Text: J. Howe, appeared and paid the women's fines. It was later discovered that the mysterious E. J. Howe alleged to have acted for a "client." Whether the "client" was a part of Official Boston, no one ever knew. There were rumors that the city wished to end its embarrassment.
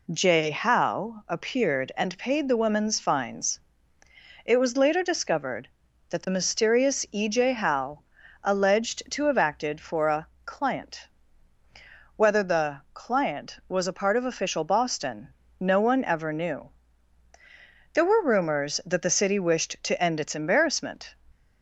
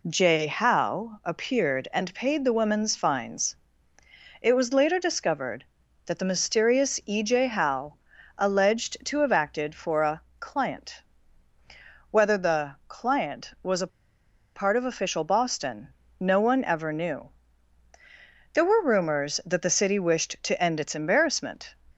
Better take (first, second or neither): first